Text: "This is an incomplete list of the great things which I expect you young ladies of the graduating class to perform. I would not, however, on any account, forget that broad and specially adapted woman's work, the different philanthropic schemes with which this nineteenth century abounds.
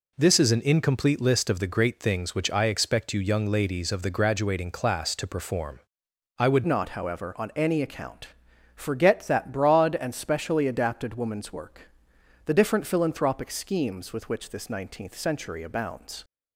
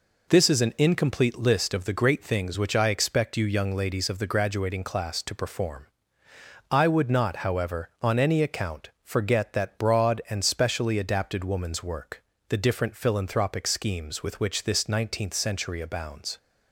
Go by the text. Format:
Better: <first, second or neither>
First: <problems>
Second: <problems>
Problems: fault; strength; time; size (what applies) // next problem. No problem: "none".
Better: second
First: changes voice at "not"; from 6.6 s on; 9.6 s long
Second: none